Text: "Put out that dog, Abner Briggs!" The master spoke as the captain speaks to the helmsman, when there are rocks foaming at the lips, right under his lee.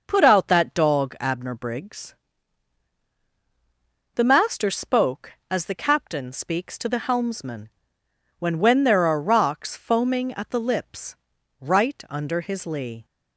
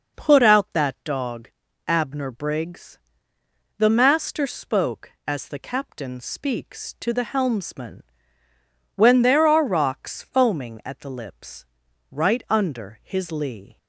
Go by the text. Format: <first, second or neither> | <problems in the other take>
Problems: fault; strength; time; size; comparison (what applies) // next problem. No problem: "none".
second | starts louder than the rest; noticeable; until 1.0 s; 6 dB // says "when" twice; at 8.5 s